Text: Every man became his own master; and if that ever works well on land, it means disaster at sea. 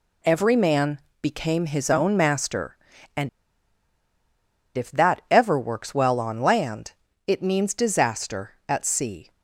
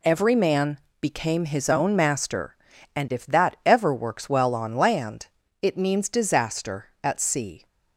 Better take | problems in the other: second | pauses between "man" and "became"; slight; at 0.9 s; 0.20 s long; slight in the second // pauses between "and" and "if"; strong; at 3.2 s; 1.4 s long

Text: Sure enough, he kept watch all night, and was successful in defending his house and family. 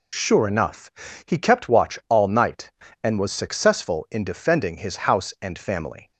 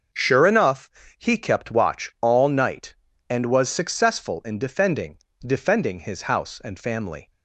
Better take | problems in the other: first | starts louder than the rest; until 1.4 s; 6.5 dB // says "defending" twice; at 5.3 s

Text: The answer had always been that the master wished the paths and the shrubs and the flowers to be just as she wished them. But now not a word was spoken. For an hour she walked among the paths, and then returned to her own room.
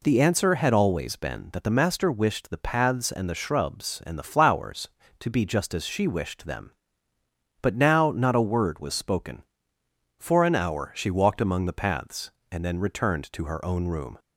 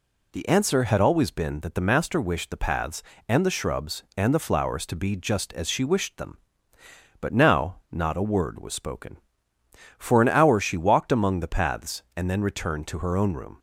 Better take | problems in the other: neither | none

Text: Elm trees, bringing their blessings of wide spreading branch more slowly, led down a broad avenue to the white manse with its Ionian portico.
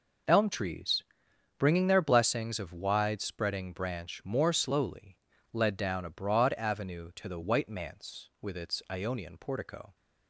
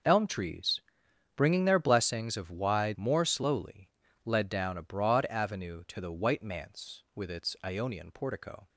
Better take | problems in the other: first | skips "spreading branch"; at 2.9 s

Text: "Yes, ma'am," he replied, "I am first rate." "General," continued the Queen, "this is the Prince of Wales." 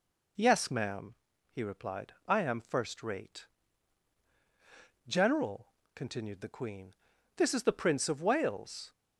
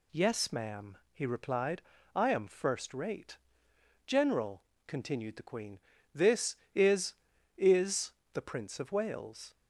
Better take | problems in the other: first | says "is" twice; at 7.5 s

